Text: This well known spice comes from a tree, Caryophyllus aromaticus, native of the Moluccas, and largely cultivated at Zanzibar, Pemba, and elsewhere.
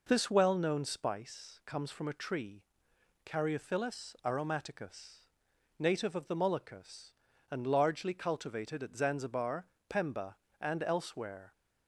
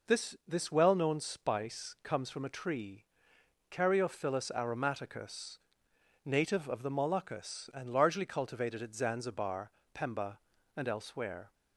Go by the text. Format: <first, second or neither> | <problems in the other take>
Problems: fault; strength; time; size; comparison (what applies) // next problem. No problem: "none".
first | says "This" twice; at 0.4 s